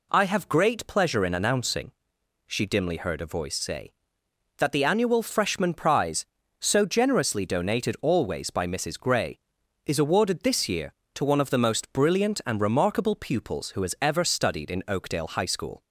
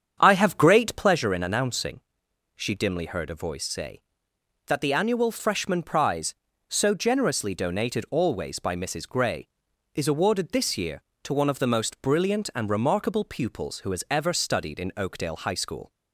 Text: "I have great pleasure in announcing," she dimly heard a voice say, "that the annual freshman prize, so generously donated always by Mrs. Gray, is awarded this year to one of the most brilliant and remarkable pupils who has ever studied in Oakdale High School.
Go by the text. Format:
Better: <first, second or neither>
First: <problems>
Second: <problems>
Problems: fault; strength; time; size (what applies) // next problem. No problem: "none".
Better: first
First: none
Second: starts louder than the rest; strong; until 1.3 s; 8 dB